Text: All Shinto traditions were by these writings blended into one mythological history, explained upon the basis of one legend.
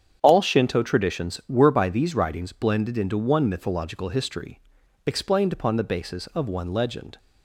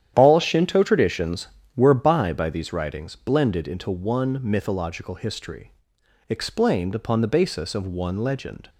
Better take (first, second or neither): first